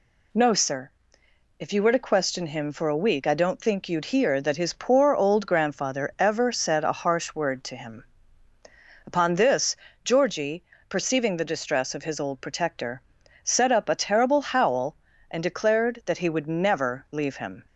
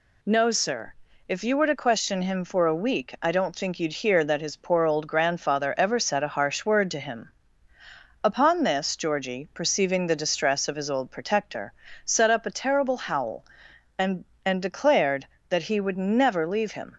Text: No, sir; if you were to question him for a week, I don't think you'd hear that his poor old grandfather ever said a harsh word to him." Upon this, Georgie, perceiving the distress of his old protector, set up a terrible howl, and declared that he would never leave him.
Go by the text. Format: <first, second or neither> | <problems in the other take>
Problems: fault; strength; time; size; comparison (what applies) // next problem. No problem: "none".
first | says "and" twice; at 14.4 s